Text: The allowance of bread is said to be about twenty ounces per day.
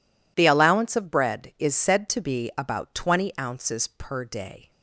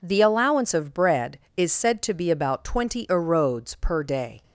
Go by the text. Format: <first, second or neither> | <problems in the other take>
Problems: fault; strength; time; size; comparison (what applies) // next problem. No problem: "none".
first | says "erodes" for "ounces"; at 3.0 s